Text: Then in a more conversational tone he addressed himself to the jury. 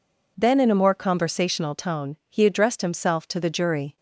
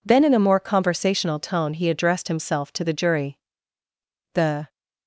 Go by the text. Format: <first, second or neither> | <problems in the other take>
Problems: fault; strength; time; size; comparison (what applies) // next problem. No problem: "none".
first | goes on to say "The"; slight; from 4.3 s on; 0.38 s long